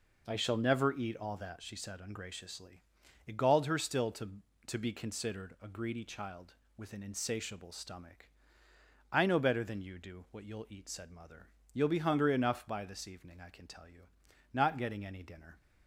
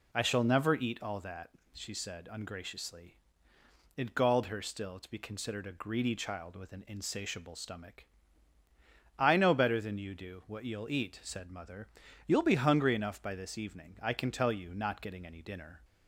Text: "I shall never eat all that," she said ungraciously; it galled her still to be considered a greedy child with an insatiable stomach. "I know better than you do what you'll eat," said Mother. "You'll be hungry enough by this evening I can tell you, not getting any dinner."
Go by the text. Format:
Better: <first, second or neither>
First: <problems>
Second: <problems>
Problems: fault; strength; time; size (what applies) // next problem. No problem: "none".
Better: second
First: says "to" twice; at 4.6 s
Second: none